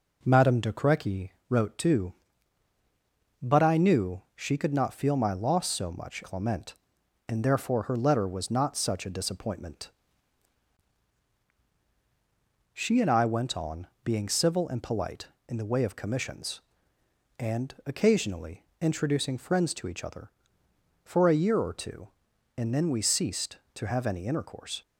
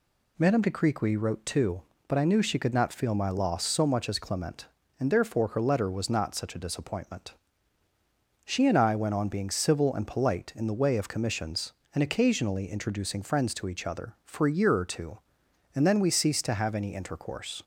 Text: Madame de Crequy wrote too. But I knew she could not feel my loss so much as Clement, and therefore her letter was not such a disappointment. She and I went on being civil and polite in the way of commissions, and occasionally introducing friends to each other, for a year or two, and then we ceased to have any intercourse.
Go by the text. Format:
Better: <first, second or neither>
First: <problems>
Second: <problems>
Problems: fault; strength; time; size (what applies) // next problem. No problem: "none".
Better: second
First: pauses between "Crequy" and "wrote"; slight; at 1.3 s; 0.18 s long // skips "as"; at 6.2 s // pauses between "on" and "being"; slight; at 13.8 s; 0.18 s long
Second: none